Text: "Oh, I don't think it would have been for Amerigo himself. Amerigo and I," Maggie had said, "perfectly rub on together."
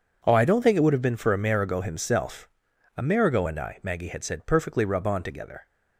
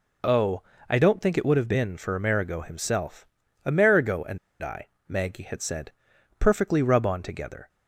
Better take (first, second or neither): first